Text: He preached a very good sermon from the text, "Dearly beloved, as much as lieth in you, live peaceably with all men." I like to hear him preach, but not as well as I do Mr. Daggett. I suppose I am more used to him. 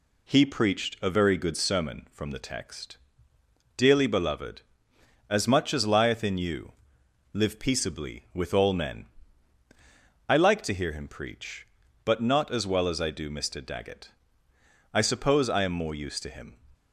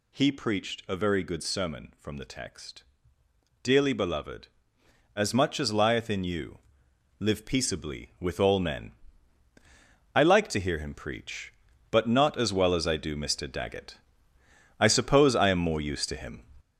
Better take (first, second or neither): first